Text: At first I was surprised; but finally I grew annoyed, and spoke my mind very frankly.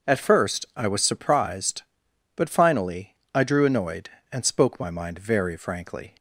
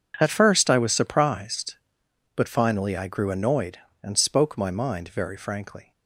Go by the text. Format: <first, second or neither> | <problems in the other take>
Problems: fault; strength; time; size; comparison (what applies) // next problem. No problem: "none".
second | pauses between "finally" and "I"; slight; at 3.1 s; 0.22 s long // says "drew" for "grew"; at 3.4 s